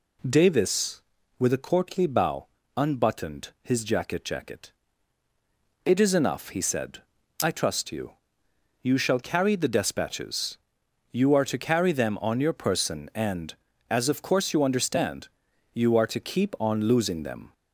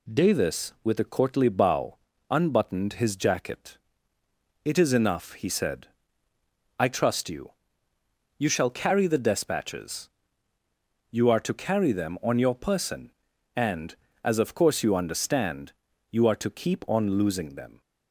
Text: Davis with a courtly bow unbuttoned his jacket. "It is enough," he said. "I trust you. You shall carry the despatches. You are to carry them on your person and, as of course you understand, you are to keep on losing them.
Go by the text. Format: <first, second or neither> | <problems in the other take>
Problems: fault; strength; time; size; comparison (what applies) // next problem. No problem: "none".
second | pauses between "bow" and "unbuttoned"; slight; at 2.4 s; 0.30 s long; slight in the second // says "jacket" twice; at 4.2 s